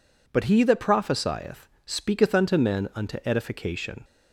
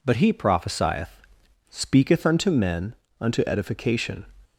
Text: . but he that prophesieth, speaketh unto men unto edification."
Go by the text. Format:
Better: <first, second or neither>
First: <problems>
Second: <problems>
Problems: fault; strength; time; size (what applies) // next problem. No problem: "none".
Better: first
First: none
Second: skips "that"; at 0.3 s // pauses between "men" and "unto"; slight; at 2.9 s; 0.24 s long